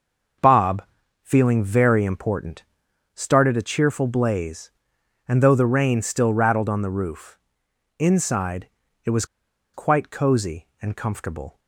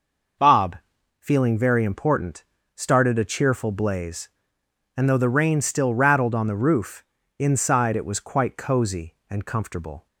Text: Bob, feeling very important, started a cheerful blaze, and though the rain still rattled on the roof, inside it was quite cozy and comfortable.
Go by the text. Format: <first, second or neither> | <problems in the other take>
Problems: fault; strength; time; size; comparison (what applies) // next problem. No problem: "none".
second | starts louder than the rest; until 1.8 s; 6 dB // pauses between "inside" and "it"; slight; at 8.6 s; 0.36 s long // pauses between "was" and "quite"; noticeable; at 9.2 s; 0.49 s long